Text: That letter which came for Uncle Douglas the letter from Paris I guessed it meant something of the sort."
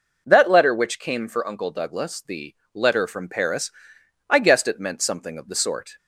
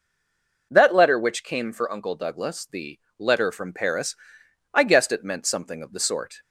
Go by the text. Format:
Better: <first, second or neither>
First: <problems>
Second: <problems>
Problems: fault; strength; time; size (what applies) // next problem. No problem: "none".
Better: first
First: pauses between "the" and "letter"; slight; at 2.5 s; 0.20 s long // pauses between "Paris" and "I"; noticeable; at 3.7 s; 0.58 s long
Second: stays silent before the first word; slight; until 0.7 s; 0.7 s long // pauses between "the" and "letter"; slight; at 2.9 s; 0.20 s long // pauses between "Paris" and "I"; noticeable; at 4.1 s; 0.58 s long